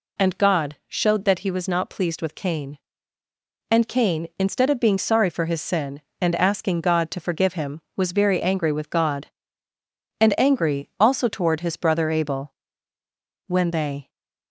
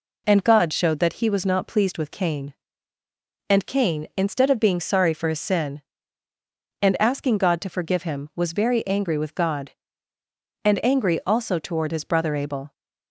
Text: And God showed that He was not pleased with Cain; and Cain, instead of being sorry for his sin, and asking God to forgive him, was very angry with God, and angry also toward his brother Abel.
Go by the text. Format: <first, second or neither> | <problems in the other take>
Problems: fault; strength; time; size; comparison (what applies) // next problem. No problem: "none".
second | goes on to say "When they"; noticeable; from 13.4 s on; 0.62 s long